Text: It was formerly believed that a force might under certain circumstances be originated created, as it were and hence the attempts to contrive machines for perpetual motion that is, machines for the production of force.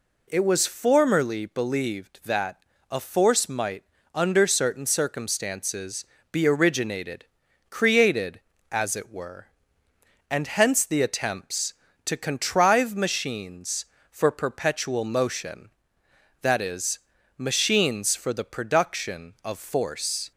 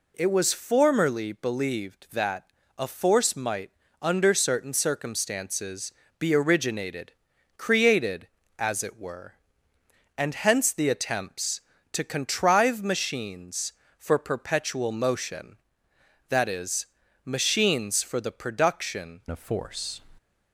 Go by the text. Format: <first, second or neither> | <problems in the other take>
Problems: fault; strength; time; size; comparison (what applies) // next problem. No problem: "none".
first | pauses between "that" and "a"; slight; at 2.4 s; 0.32 s long; slight in the first // pauses between "might" and "under"; slight; at 3.7 s; 0.30 s long; slight in the first // pauses between "circumstances" and "be"; slight; at 5.9 s; 0.28 s long; slight in the first // pauses between "originated" and "created"; at 7.1 s; 0.44 s long; also in the first // changes voice at "of"; from 19.3 s on; 0.7 s long